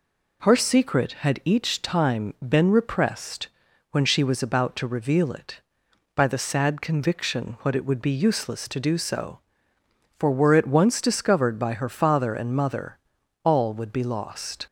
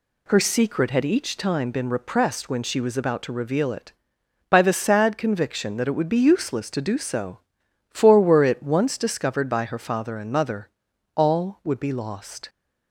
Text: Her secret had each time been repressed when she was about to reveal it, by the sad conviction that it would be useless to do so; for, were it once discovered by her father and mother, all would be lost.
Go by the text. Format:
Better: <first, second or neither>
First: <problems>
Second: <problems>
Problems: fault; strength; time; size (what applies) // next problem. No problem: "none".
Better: second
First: pauses between "repressed" and "when"; at 3.4 s; 0.44 s long // says "what" for "that"; at 7.6 s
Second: none